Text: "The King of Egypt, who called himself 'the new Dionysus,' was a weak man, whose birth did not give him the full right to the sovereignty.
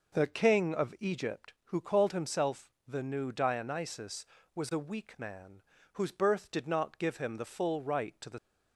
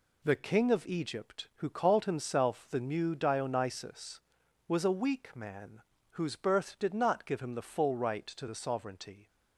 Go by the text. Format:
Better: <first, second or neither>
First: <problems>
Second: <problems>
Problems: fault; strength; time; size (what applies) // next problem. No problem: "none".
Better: second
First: pauses between "himself" and "the"; slight; at 2.6 s; 0.16 s long // stops before "sovereignty"; at 8.3 s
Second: none